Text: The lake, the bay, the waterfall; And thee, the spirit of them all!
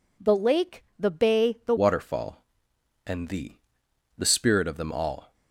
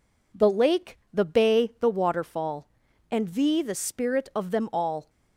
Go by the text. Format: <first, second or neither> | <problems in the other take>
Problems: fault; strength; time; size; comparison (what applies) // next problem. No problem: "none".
second | changes voice at "waterfall"; from 1.7 s on; 3.6 s long